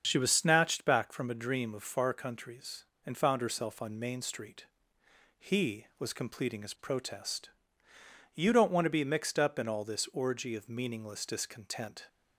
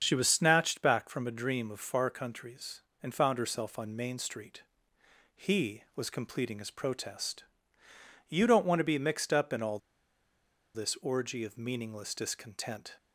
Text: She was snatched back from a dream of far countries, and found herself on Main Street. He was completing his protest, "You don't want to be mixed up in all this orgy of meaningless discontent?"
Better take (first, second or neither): first